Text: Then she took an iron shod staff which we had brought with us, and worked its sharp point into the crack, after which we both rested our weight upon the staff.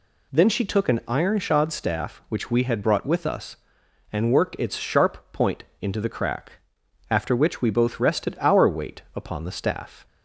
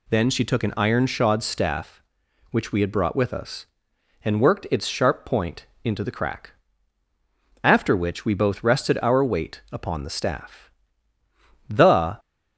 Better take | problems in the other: first | pauses between "point" and "into"; slight; at 5.6 s; 0.18 s long; slight in the first // goes on to say "The"; from 11.6 s on; 0.50 s long

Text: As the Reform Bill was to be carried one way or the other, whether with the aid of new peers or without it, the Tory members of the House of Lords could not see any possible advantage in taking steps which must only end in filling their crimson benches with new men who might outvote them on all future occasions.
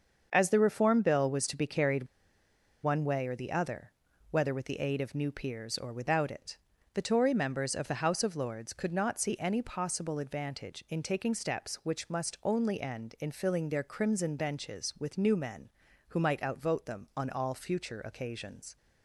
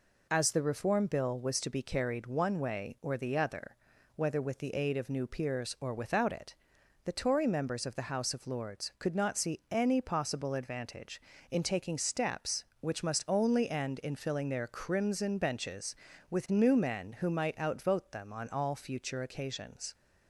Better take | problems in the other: second | starts louder than the rest; until 1.3 s; 6.5 dB // pauses between "carried" and "one"; noticeable; at 2.0 s; 0.77 s long

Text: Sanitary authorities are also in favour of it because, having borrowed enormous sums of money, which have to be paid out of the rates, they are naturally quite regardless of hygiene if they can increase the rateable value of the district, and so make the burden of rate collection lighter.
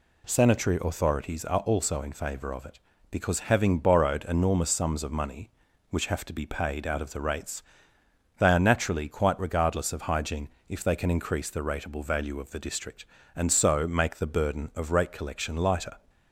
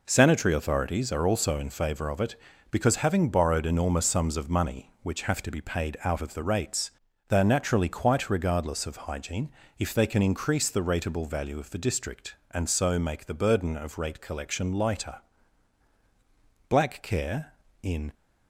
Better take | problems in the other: first | pauses between "hygiene" and "if"; slight; at 9.4 s; 0.28 s long; slight in the first // goes on to say "Black care in"; from 16.6 s on; 1.4 s long

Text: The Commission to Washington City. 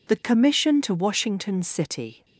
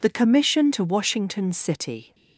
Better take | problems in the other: neither | none

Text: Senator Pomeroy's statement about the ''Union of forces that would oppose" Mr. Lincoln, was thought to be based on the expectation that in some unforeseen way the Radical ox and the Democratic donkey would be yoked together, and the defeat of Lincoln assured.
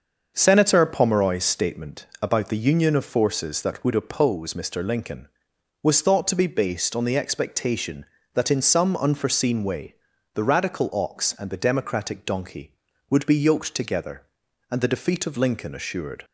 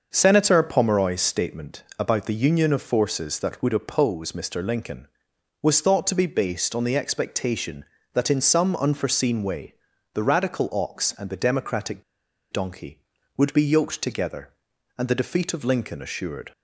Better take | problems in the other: first | starts louder than the rest; until 1.1 s; 6.5 dB; also in the first // pauses between "way" and "the"; at 9.7 s; 0.40 s long; also in the first // pauses between "Democratic" and "donkey"; noticeable; at 12.0 s; 0.48 s long

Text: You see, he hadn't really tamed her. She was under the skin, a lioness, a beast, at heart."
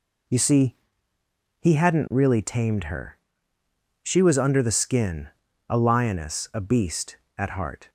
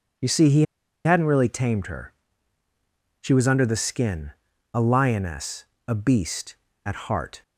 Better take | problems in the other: first | pauses between "he" and "hadn't"; at 0.6 s; 0.42 s long

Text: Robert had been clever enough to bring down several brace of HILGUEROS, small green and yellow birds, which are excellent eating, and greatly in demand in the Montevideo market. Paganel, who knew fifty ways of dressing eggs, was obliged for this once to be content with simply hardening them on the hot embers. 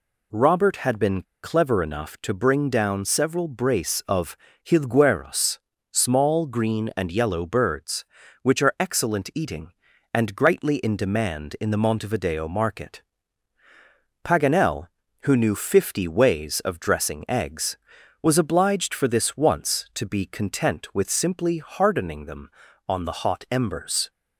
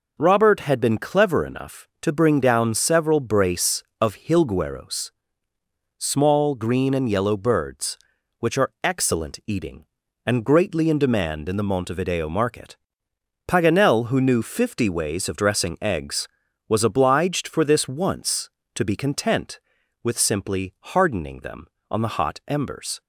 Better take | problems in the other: second | pauses between "been" and "clever"; slight; at 1.2 s; 0.20 s long // pauses between "of" and "HILGUEROS"; slight; at 4.3 s; 0.30 s long

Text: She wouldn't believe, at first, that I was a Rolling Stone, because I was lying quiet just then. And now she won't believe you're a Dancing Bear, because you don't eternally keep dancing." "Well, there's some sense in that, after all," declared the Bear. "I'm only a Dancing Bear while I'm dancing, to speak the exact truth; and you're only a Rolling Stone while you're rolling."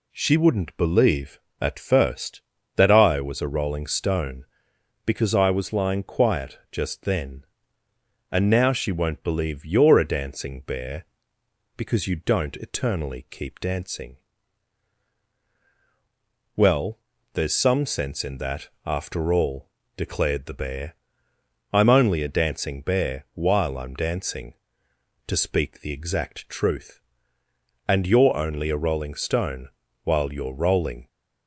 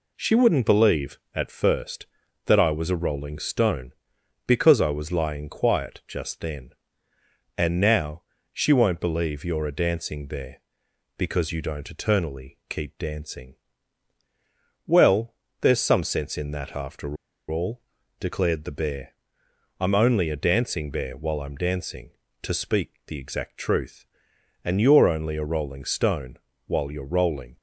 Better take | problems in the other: first | pauses between "now" and "she"; slight; at 8.2 s; 0.30 s long // pauses between "after" and "all"; slight; at 17.1 s; 0.34 s long // pauses between "Stone" and "while"; slight; at 26.3 s; 0.30 s long; slight in the first

